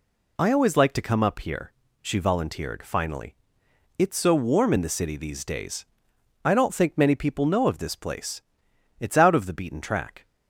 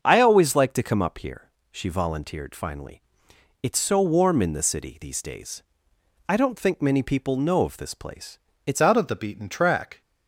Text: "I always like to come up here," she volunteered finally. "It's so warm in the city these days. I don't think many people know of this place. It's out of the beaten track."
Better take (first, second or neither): first